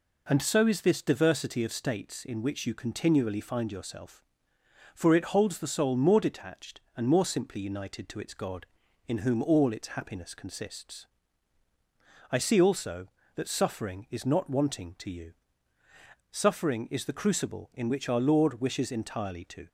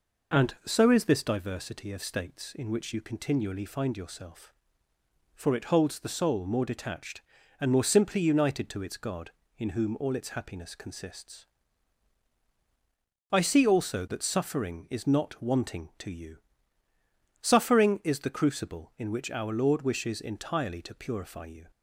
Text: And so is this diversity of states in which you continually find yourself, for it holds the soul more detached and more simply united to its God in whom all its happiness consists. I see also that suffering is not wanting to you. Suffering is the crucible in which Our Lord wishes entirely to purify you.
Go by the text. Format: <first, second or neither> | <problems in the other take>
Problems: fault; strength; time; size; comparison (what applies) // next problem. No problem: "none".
second | stops before "purify you"; at 19.6 s